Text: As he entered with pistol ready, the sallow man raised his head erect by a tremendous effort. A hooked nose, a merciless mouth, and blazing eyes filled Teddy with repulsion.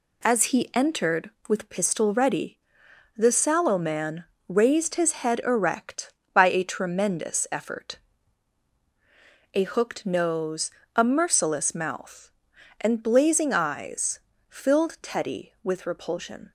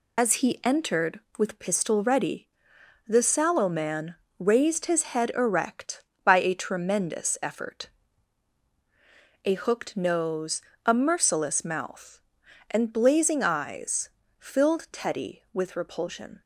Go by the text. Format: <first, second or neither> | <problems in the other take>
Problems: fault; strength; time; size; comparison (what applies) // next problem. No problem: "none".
first | loses the start of "As"; at 0.1 s; 60 ms // pauses between "man" and "raised"; slight; at 4.1 s; 0.22 s long; slight in the first // pauses between "eyes" and "filled"; slight; at 14.0 s; 0.28 s long; slight in the first